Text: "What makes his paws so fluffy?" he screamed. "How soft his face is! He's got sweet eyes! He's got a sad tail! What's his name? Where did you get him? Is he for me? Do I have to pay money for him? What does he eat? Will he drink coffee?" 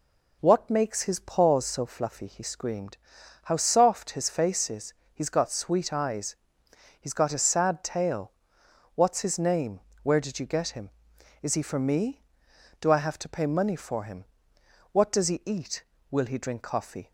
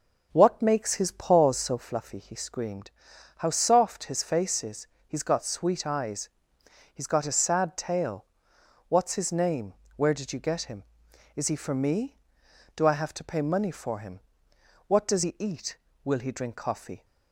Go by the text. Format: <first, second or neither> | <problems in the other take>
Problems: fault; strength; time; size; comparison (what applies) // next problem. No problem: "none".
first | starts louder than the rest; noticeable; until 1.9 s; 6 dB